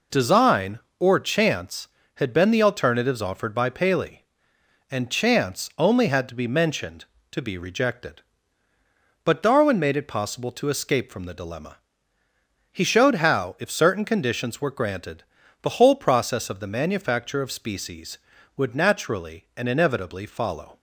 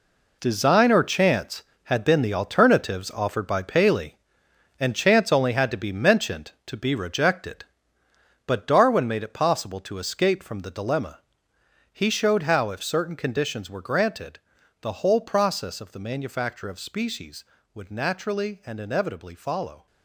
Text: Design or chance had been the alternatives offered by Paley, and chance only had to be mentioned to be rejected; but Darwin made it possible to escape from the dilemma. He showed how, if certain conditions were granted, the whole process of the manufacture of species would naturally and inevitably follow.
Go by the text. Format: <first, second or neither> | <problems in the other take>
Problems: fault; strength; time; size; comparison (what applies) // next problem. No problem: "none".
first | gets quieter; strong; throughout; 11 dB